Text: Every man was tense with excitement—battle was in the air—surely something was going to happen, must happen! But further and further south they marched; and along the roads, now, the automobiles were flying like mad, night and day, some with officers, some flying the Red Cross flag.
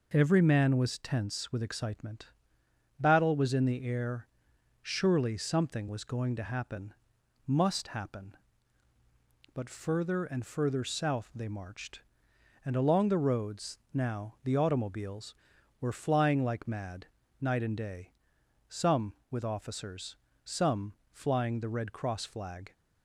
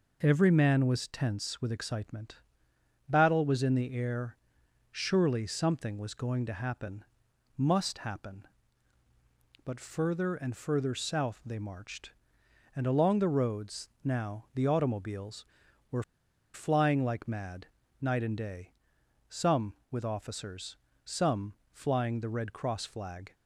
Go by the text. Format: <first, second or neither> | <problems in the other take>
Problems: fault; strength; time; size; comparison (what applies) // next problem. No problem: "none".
first | pauses between "were" and "flying"; noticeable; at 16.0 s; 0.50 s long // pauses between "some" and "flying"; slight; at 21.5 s; 0.20 s long; slight in the first